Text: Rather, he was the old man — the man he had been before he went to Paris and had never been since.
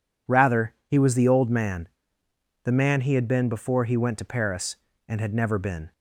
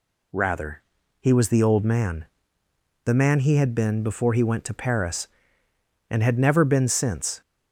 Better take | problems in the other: second | stops before "since"; at 5.9 s

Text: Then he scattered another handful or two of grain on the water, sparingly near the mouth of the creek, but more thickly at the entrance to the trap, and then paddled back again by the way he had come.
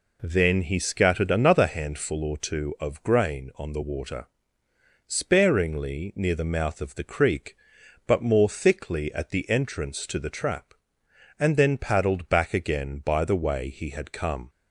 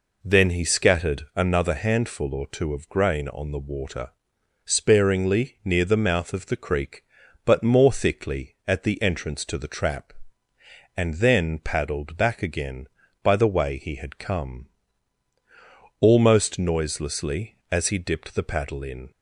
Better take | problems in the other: first | goes on to say "Almost noiselessly as he dipped the paddle in"; strong; from 16.0 s on; 3.1 s long

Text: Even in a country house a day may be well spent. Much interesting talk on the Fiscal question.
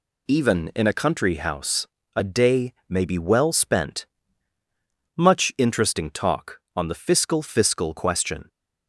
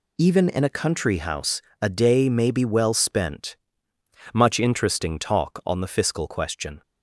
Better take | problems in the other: second | pauses between "house" and "a"; slight; at 1.8 s; 0.30 s long; slight in the second // pauses between "day" and "may"; slight; at 2.7 s; 0.16 s long // says "Fiscal" twice; at 7.4 s

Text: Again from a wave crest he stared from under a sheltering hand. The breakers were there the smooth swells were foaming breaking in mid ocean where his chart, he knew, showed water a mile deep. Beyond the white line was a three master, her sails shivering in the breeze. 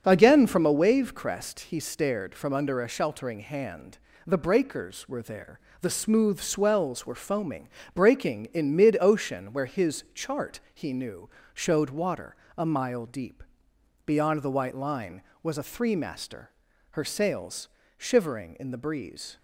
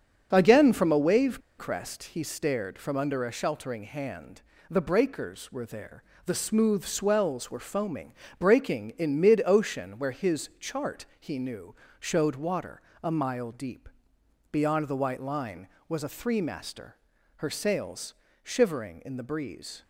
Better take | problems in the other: first | starts louder than the rest; until 1.3 s; 7 dB; also in the first // pauses between "wave" and "crest"; slight; at 1.4 s; 0.17 s long // pauses between "there" and "the"; slight; at 6.0 s; 0.22 s long; slight in the first // pauses between "foaming" and "breaking"; slight; at 8.1 s; 0.24 s long; slight in the first // pauses between "water" and "a"; slight; at 12.8 s; 0.22 s long; slight in the first // pauses between "sails" and "shivering"; slight; at 18.1 s; 0.28 s long; slight in the first

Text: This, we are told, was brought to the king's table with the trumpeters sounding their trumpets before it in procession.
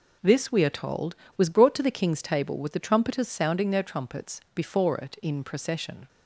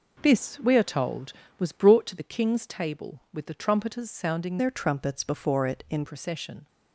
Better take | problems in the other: first | changes voice from "their" to "in"; from 4.5 to 6.0 s; 1.5 s long

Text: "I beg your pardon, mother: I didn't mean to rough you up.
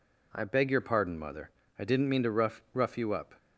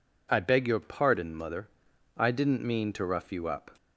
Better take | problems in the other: second | says "rough" twice; at 2.7 s

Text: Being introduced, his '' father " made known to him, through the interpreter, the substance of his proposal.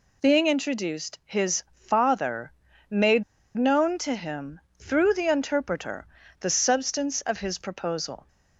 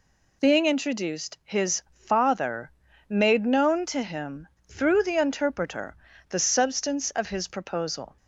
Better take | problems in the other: second | pauses between "made" and "known"; slight; at 3.2 s; 0.33 s long

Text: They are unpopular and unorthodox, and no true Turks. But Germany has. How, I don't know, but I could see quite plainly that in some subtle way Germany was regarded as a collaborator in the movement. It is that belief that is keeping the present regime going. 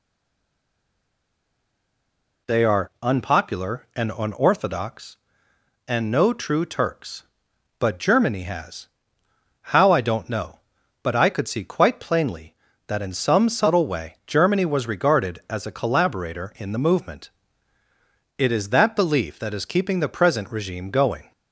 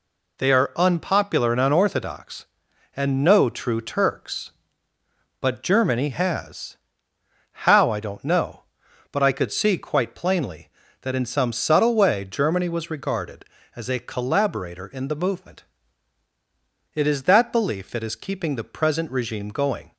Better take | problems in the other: second | stays silent before the first word; until 2.4 s; 2.4 s long

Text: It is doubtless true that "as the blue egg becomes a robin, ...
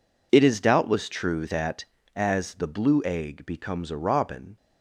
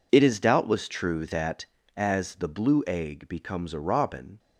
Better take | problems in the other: neither | none

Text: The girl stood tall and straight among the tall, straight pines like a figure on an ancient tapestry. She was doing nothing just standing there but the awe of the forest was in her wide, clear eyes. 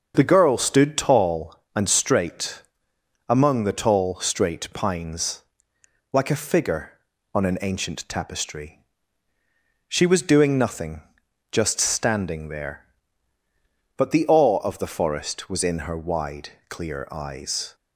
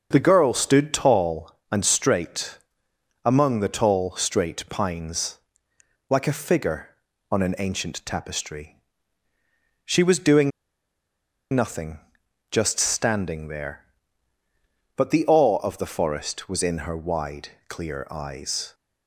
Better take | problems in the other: first | starts louder than the rest; until 1.1 s; 6.5 dB; also in the first // pauses between "straight" and "among"; noticeable; at 2.5 s; 0.66 s long; noticeable in the first // pauses between "pines" and "like"; noticeable; at 5.3 s; 0.72 s long; noticeable in the first // pauses between "doing" and "nothing"; at 10.5 s; 1.0 s long // pauses between "nothing" and "just"; noticeable; at 11.9 s; 0.52 s long; noticeable in the first

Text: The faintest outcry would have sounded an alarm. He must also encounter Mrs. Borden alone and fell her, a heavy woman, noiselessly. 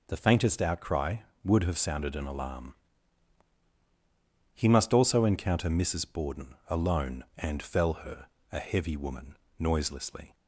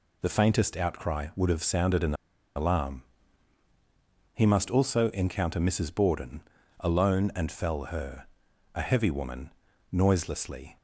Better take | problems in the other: first | pauses between "an" and "alarm"; at 2.1 s; 0.40 s long // pauses between "Borden" and "alone"; at 6.4 s; 0.38 s long

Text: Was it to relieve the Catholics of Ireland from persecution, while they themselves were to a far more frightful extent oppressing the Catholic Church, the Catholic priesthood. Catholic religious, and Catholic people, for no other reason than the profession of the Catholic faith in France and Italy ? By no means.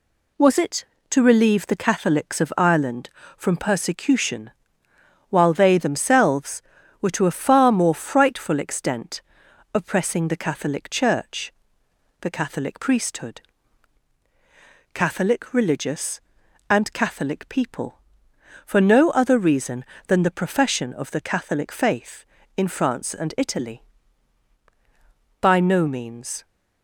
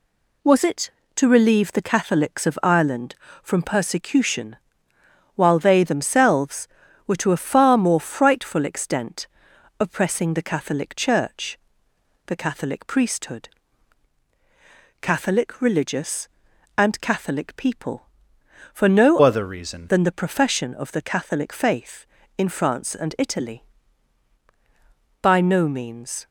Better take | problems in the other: first | pauses between "extent" and "oppressing"; noticeable; at 9.2 s; 0.52 s long; noticeable in the first // changes voice from "other" to "reason"; from 19.2 to 19.8 s; 0.6 s long

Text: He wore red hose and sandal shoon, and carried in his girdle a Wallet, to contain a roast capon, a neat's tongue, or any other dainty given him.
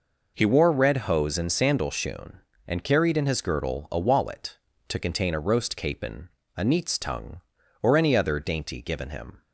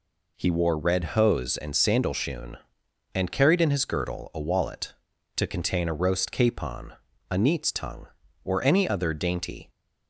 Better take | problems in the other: first | stops before "given him"; at 9.6 s

